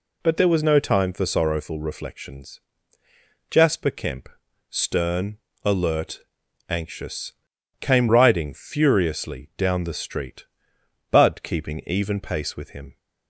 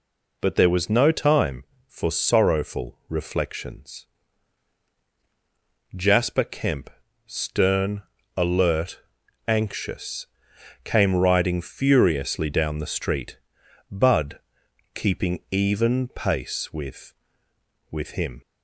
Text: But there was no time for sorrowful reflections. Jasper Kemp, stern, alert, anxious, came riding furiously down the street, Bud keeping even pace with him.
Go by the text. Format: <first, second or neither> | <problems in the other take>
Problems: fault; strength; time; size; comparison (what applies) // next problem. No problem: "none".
first | pauses between "Bud" and "keeping"; noticeable; at 14.3 s; 0.56 s long // says "with" twice; at 17.9 s